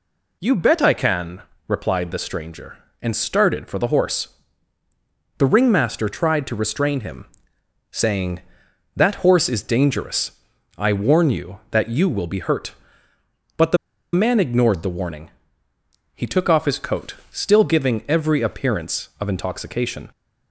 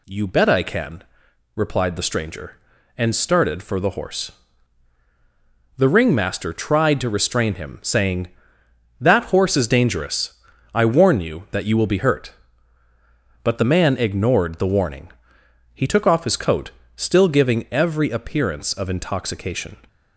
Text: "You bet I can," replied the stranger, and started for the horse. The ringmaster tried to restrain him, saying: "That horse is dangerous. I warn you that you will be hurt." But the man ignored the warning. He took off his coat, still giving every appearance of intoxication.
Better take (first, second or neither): second